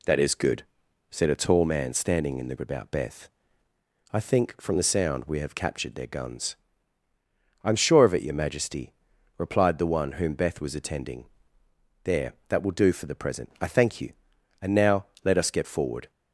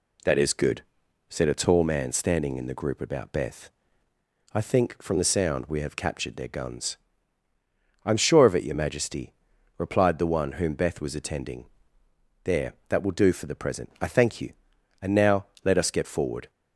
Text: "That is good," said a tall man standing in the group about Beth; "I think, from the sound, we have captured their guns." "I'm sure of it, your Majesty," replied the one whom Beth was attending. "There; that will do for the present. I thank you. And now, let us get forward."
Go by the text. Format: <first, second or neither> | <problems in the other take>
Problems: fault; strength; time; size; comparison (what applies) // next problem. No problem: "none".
second | skips "group"; at 2.5 s